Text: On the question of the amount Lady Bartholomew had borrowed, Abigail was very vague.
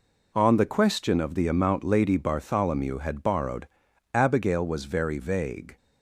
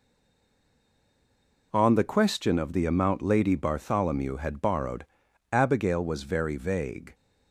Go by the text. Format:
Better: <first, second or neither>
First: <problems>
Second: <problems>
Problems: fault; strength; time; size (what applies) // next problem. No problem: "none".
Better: first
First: none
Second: stays silent before the first word; noticeable; until 1.7 s; 1.7 s long